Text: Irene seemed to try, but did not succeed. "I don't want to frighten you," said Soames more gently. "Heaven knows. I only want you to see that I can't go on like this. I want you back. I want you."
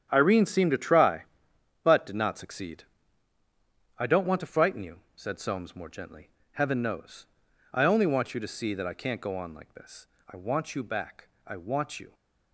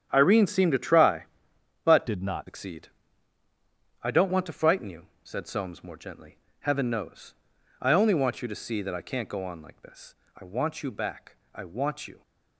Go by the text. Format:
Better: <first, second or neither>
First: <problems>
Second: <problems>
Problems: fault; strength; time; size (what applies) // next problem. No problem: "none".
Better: first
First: starts louder than the rest; strong; until 1.1 s; 9 dB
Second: starts louder than the rest; strong; until 1.1 s; 9.5 dB // changes voice from "did" to "not"; from 2.0 to 2.4 s; 0.4 s long